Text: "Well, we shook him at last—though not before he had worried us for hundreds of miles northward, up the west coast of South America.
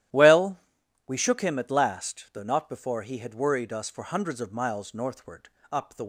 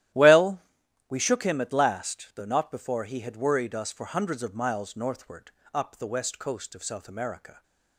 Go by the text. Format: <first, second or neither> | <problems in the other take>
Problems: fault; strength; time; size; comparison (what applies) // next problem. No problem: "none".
second | starts louder than the rest; strong; until 1.6 s; 12.5 dB; strong in the second // stops before "west coast of South America"; at 6.0 s